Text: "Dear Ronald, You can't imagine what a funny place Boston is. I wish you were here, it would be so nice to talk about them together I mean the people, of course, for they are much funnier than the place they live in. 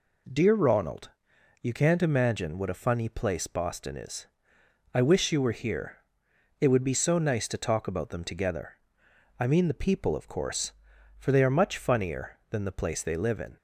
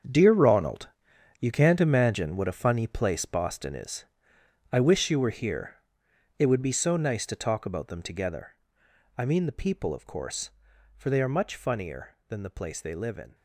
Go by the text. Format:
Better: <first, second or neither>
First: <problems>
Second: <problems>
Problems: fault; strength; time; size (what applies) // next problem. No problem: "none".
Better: first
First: pauses between "together" and "I"; noticeable; at 8.7 s; 0.64 s long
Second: gets quieter; strong; throughout; 12 dB // pauses between "together" and "I"; noticeable; at 8.5 s; 0.64 s long